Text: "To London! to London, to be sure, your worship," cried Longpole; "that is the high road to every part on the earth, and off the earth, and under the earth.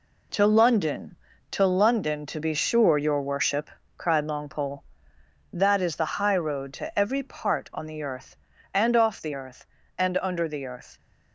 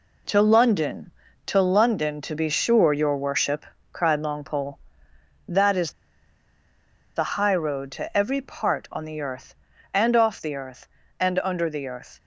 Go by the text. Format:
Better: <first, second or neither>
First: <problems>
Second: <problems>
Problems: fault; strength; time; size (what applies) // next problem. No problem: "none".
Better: first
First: none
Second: pauses between "is" and "the"; at 5.9 s; 1.2 s long